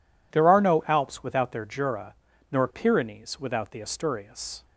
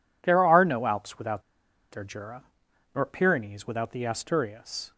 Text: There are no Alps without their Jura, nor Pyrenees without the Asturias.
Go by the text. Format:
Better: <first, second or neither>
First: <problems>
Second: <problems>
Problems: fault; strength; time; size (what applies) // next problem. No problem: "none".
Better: first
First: none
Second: pauses between "without" and "their"; noticeable; at 1.4 s; 0.49 s long